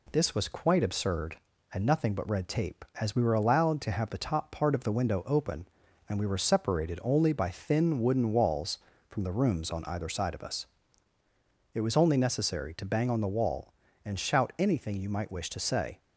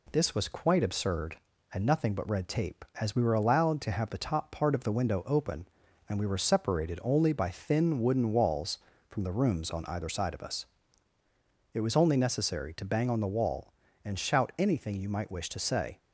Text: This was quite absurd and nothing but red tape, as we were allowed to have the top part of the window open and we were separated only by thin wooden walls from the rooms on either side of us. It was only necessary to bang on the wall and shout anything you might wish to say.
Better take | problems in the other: neither | none

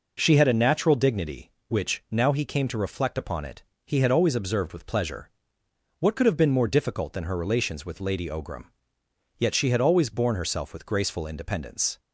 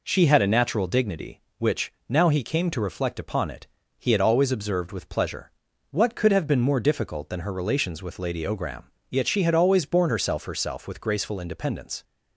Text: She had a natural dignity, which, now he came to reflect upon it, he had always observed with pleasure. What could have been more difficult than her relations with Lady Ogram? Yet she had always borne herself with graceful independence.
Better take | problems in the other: first | says "herself" twice; at 10.4 s

